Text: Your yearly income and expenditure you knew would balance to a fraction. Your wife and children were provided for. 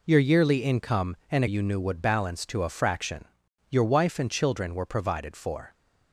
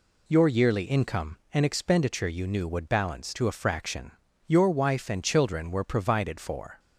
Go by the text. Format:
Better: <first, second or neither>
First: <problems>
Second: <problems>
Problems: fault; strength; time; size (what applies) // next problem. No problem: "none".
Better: second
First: skips "expenditure"; at 1.4 s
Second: none